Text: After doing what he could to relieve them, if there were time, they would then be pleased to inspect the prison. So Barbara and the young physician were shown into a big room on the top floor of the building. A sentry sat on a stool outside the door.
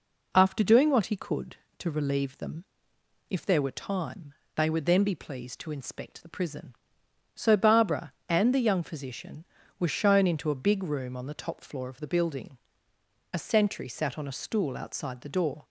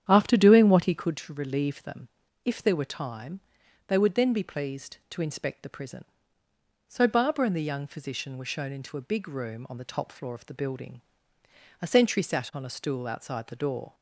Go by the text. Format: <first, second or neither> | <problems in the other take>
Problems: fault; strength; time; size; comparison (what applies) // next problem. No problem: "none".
first | starts louder than the rest; strong; until 1.3 s; 9.5 dB